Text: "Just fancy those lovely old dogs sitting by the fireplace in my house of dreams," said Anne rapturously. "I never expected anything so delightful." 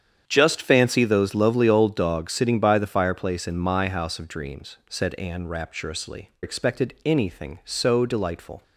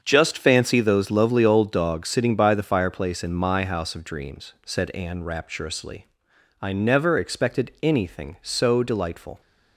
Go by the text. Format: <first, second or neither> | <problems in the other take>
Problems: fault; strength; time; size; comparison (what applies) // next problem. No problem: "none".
second | starts louder than the rest; strong; until 1.2 s; 8.5 dB; also in the second // skips "I never"; at 6.3 s